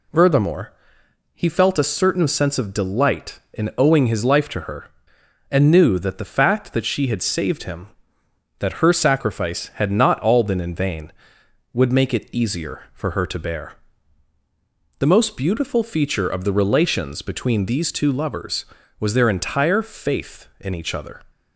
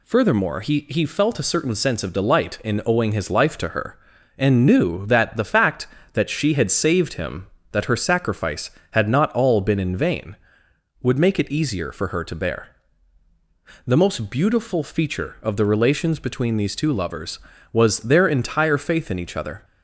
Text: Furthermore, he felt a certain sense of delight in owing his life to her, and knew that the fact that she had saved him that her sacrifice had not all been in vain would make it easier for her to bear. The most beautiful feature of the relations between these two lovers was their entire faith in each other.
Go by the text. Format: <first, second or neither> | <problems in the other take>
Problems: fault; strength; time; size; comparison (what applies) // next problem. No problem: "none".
first | says "he" twice; at 0.8 s